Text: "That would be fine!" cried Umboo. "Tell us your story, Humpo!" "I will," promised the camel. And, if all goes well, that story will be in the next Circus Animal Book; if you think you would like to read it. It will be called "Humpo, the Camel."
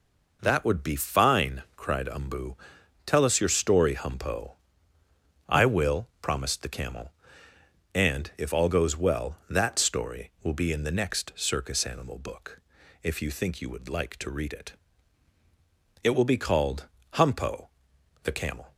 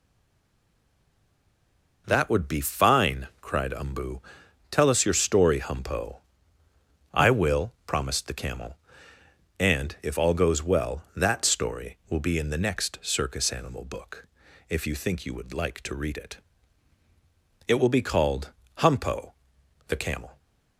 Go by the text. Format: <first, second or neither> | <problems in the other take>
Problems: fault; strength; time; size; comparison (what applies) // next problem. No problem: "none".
first | stays silent before the first word; noticeable; until 2.0 s; 2.0 s long // pauses between "called" and "Humpo"; slight; at 18.5 s; 0.24 s long; slight in the first